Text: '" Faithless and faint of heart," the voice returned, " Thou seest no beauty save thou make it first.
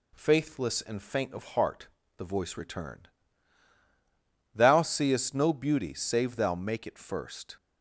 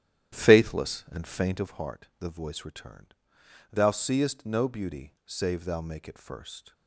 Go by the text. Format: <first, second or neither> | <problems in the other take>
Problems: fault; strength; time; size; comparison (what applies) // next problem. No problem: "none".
first | starts louder than the rest; strong; until 1.8 s; 11 dB